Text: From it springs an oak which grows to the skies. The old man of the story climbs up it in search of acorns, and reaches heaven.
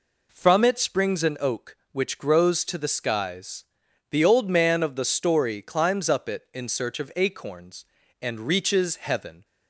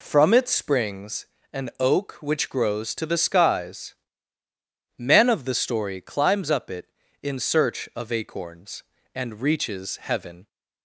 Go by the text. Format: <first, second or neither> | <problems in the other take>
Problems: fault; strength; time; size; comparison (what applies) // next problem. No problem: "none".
first | pauses between "springs" and "an"; slight; at 1.2 s; 0.28 s long // skips "The old"; at 4.4 s